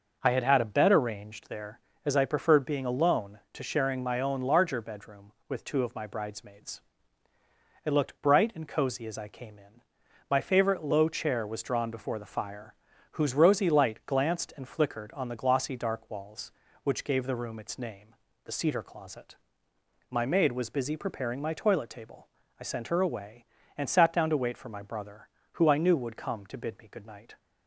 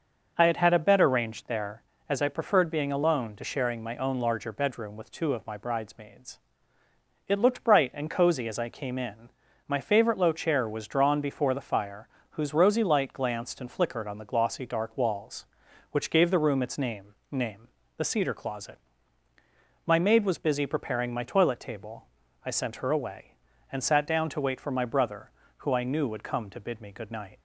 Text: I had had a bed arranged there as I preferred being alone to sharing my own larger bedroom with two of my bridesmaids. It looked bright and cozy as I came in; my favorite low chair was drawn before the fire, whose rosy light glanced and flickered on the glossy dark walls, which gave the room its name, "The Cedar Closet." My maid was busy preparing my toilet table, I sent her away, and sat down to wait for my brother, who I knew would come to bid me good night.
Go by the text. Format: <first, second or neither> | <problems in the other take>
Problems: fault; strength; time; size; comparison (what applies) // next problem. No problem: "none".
first | starts louder than the rest; until 1.3 s; 6 dB // says "name" twice; at 17.3 s